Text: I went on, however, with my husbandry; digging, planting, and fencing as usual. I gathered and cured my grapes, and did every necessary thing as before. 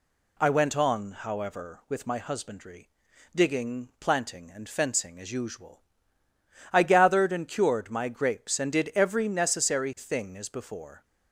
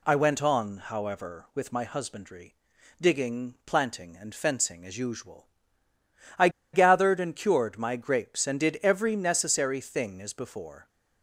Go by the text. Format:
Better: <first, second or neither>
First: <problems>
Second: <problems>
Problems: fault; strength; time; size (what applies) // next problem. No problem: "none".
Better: first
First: none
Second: pauses between "I" and "gathered"; slight; at 6.4 s; 0.24 s long